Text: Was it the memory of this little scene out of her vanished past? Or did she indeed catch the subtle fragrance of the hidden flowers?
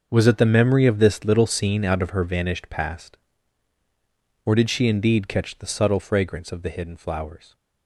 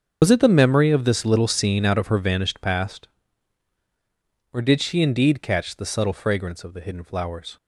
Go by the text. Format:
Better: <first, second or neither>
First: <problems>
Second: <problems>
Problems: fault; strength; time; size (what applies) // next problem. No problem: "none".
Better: first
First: starts louder than the rest; until 1.1 s; 6.5 dB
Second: loses the start of "Was"; at 0.2 s; 75 ms // starts louder than the rest; until 1.2 s; 6.5 dB